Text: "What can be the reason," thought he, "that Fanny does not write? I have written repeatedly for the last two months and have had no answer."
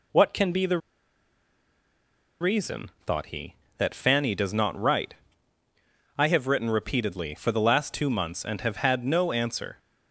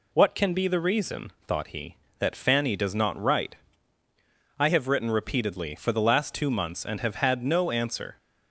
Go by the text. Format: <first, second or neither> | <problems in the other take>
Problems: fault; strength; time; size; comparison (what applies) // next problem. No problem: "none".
second | pauses between "the" and "reason"; strong; at 0.7 s; 1.6 s long